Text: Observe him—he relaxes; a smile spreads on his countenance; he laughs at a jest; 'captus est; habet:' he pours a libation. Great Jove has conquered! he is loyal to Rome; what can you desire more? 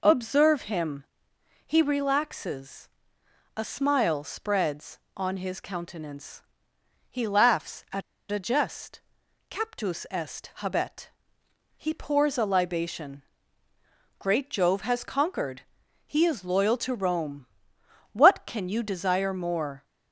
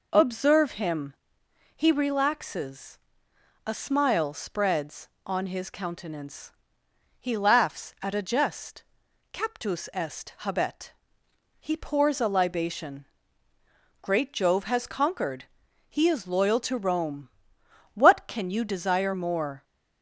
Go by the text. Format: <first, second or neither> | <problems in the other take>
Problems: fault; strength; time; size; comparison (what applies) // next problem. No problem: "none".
second | pauses between "at" and "a"; slight; at 8.0 s; 0.29 s long